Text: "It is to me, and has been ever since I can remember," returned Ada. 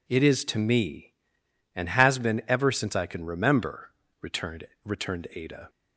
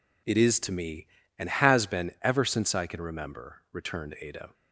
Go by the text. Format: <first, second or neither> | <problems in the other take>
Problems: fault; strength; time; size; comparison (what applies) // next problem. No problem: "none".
second | says "returned" twice; at 4.8 s